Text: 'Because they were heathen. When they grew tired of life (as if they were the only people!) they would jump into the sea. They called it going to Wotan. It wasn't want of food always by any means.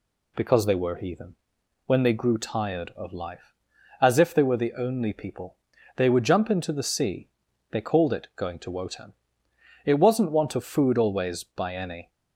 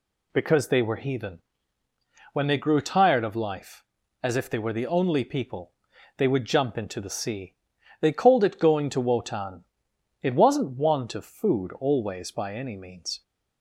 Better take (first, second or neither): second